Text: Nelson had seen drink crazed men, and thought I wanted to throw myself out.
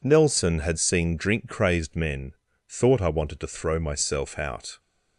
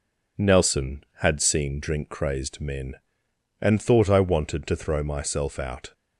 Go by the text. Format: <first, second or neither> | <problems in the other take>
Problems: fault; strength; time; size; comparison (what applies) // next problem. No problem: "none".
second | skips "and"; at 2.4 s